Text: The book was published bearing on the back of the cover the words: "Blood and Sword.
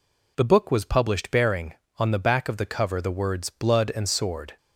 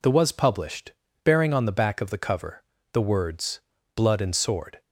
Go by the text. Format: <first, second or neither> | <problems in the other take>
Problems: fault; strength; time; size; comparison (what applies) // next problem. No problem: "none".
first | skips "book"; at 0.1 s // pauses between "published" and "bearing"; slight; at 0.9 s; 0.32 s long // pauses between "cover" and "the"; slight; at 2.6 s; 0.30 s long